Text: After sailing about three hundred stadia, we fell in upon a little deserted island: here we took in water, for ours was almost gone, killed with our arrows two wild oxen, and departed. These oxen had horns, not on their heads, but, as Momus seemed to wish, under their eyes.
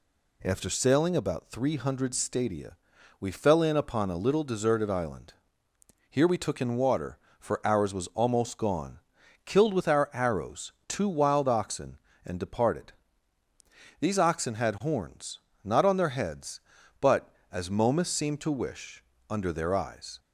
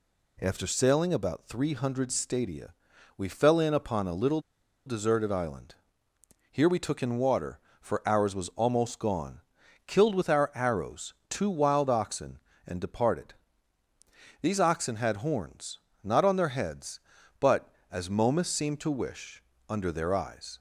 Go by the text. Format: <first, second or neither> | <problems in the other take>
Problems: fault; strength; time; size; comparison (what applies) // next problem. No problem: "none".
first | pauses between "little" and "deserted"; noticeable; at 4.3 s; 0.46 s long // pauses between "arrows" and "two"; slight; at 11.1 s; 0.16 s long; slight in the first